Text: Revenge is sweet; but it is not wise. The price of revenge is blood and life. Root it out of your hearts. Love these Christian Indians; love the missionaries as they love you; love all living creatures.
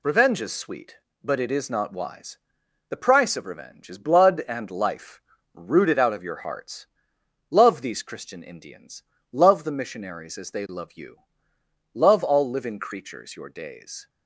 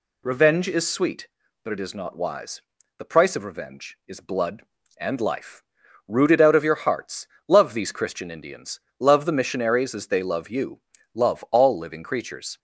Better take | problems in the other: second | goes on to say "Your days"; noticeable; from 13.3 s on; 0.72 s long

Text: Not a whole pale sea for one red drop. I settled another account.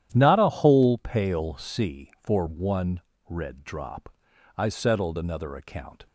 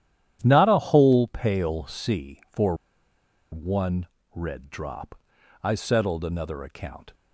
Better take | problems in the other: first | starts louder than the rest; strong; until 1.4 s; 11 dB; strong in the first // pauses between "for" and "one"; noticeable; at 2.7 s; 0.77 s long // pauses between "one" and "red"; slight; at 4.0 s; 0.28 s long; slight in the first

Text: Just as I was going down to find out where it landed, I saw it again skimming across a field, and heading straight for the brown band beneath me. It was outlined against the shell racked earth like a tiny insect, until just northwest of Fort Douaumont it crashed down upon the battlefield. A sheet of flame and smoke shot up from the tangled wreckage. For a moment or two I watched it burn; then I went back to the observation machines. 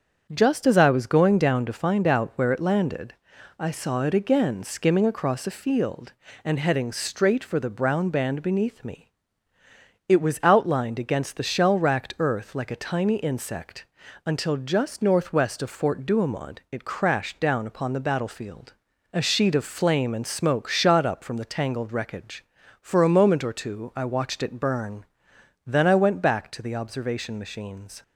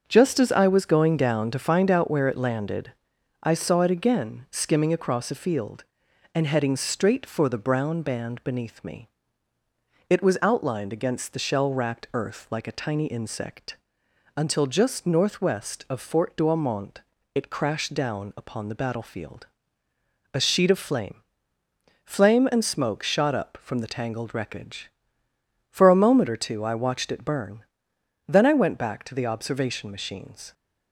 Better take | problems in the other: first | starts louder than the rest; until 1.0 s; 7 dB; also in the first // pauses between "Douaumont" and "it"; slight; at 17.0 s; 0.32 s long // says "flame" twice; at 22.0 s

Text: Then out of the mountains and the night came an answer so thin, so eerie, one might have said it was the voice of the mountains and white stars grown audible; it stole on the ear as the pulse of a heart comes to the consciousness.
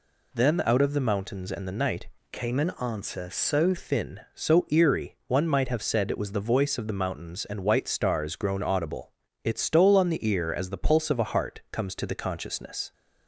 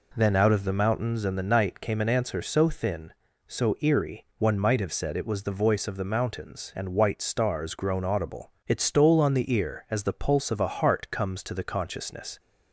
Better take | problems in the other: second | changes voice from "came" to "so"; from 2.3 to 3.7 s; 1.4 s long

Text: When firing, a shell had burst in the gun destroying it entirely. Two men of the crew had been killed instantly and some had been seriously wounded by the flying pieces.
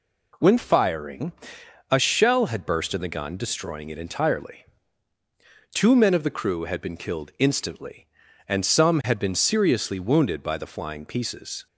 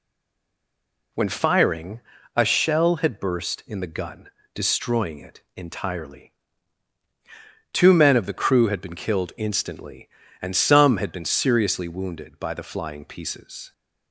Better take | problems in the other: first | stays silent before the first word; until 1.1 s; 1.1 s long // pauses between "gun" and "destroying"; slight; at 4.2 s; 0.26 s long

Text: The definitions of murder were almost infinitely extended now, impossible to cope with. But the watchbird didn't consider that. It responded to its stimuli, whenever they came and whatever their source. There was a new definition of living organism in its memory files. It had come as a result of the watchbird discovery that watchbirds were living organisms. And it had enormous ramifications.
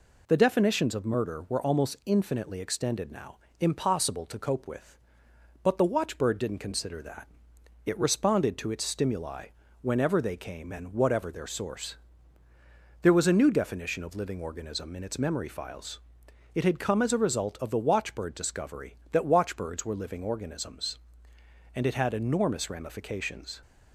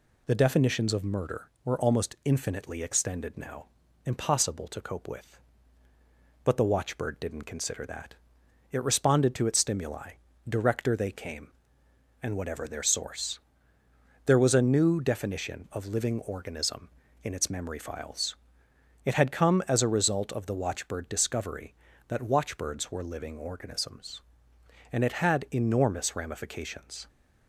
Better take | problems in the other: first | says "director" for "whenever"; at 10.4 s

